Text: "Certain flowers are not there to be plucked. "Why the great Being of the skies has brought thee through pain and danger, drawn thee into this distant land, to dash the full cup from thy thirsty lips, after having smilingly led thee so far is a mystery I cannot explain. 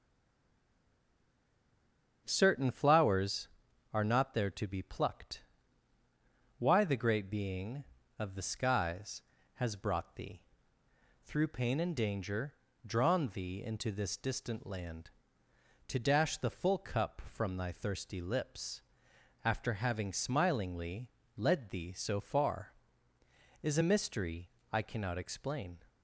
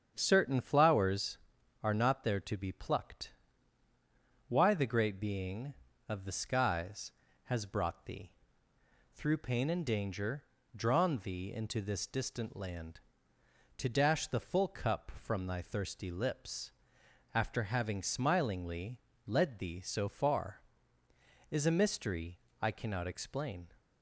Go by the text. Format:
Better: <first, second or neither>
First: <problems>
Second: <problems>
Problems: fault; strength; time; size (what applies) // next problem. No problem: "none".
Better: second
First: stays silent before the first word; until 2.2 s; 2.2 s long // starts louder than the rest; strong; until 3.2 s; 8 dB // pauses between "thee" and "through"; noticeable; at 10.4 s; 0.86 s long // pauses between "smilingly" and "led"; slight; at 21.1 s; 0.26 s long // pauses between "mystery" and "I"; slight; at 24.4 s; 0.22 s long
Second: starts louder than the rest; strong; until 1.1 s; 8 dB // pauses between "thee" and "through"; noticeable; at 8.3 s; 0.86 s long // pauses between "smilingly" and "led"; slight; at 19.0 s; 0.26 s long // pauses between "mystery" and "I"; slight; at 22.3 s; 0.22 s long